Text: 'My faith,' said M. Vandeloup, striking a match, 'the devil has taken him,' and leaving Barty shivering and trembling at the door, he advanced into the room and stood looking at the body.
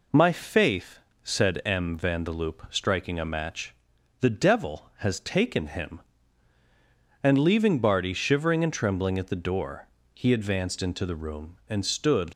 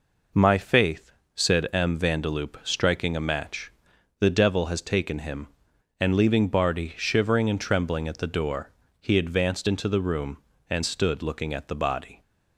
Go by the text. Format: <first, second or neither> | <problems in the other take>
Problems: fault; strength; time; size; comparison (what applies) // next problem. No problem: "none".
second | stops before "looking at the body"; at 12.3 s